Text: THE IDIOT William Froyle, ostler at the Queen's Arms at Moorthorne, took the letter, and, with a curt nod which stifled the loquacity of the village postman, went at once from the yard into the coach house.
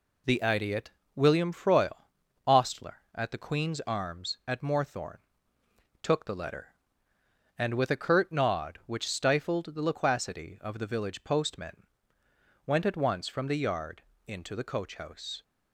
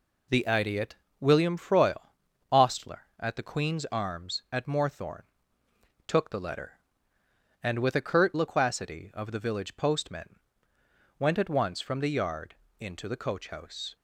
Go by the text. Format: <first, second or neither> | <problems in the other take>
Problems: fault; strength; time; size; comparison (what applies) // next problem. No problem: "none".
first | pauses between "IDIOT" and "William"; slight; at 0.9 s; 0.26 s long; slight in the first // skips "nod which stifled the"; at 8.3 s // pauses between "yard" and "into"; slight; at 12.5 s; 0.26 s long; slight in the first